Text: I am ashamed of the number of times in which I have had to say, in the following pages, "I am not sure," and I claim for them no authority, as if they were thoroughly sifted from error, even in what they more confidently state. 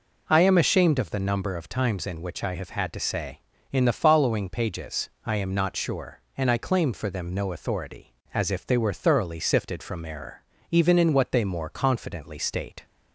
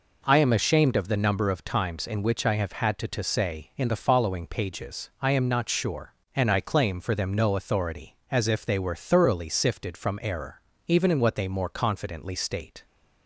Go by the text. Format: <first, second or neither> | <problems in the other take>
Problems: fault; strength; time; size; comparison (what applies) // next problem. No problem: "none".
first | says "to" twice; at 3.0 s